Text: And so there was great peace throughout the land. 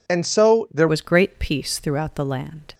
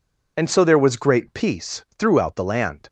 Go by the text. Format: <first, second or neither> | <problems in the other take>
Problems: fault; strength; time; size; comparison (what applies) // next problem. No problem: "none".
second | changes voice at "was"; from 0.8 s on; 1.9 s long